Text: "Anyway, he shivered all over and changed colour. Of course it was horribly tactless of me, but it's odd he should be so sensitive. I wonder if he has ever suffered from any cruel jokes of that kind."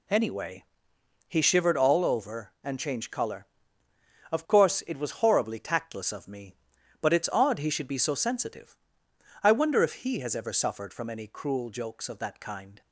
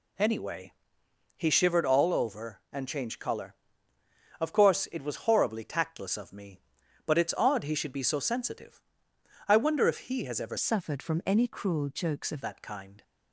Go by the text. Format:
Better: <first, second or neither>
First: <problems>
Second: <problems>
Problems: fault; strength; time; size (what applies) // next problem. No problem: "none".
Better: first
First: none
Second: changes voice from "suffered" to "of"; from 10.5 to 12.4 s; 1.9 s long